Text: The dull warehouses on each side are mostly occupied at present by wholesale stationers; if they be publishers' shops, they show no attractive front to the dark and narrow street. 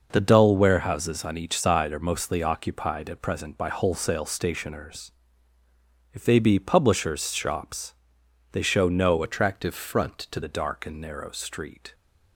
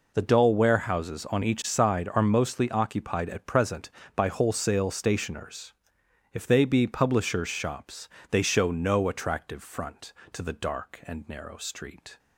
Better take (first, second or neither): second